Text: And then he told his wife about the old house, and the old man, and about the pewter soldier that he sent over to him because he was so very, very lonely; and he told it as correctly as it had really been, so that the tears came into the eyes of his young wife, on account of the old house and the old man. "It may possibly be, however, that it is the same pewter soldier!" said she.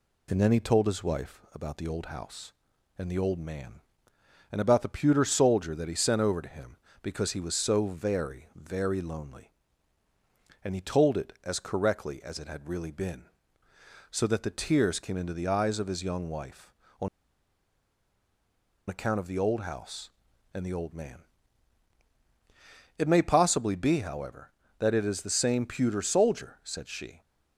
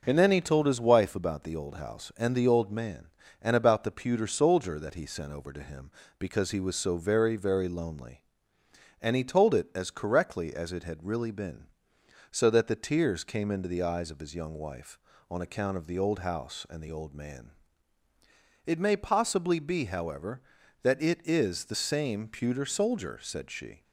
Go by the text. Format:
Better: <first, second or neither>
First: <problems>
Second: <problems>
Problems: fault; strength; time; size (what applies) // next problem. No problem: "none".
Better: second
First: pauses between "on" and "account"; strong; at 17.0 s; 1.8 s long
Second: none